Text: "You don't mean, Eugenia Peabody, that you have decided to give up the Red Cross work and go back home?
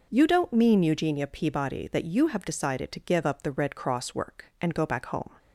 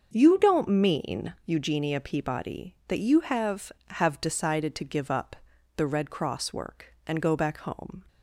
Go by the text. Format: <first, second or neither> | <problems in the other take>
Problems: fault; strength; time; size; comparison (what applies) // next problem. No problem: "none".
first | starts louder than the rest; until 1.1 s; 6.5 dB // says "have" twice; at 3.9 s // pauses between "up" and "the"; at 5.3 s; 0.42 s long